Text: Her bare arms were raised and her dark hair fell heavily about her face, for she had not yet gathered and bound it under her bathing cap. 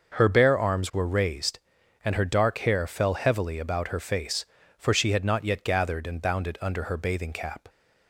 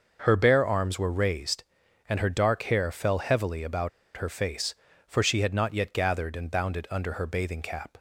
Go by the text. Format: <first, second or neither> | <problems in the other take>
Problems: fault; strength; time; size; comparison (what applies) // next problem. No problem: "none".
first | starts louder than the rest; noticeable; until 1.2 s; 6 dB; noticeable in the first // pauses between "about" and "her"; slight; at 3.8 s; 0.27 s long